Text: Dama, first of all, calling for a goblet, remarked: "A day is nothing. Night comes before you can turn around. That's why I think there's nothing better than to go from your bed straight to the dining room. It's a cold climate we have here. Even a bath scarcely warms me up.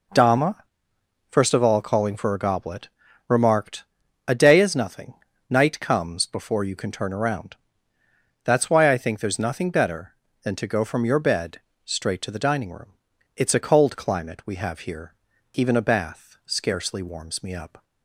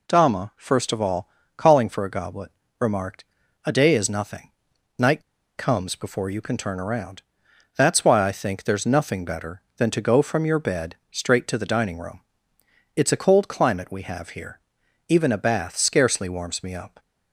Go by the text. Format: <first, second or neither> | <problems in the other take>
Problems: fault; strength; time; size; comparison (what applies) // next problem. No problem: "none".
first | pauses between "Night" and "comes"; slight; at 5.2 s; 0.35 s long // pauses between "bed" and "straight"; slight; at 10.9 s; 0.16 s long; slight in the first